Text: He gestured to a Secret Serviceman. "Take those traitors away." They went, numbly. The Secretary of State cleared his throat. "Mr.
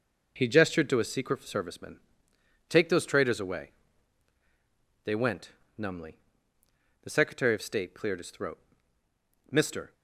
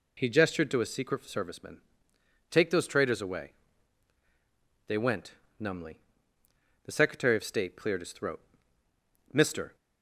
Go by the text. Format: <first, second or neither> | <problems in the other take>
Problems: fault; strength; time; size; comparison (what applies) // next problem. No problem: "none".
second | gets quieter; strong; throughout; 8.5 dB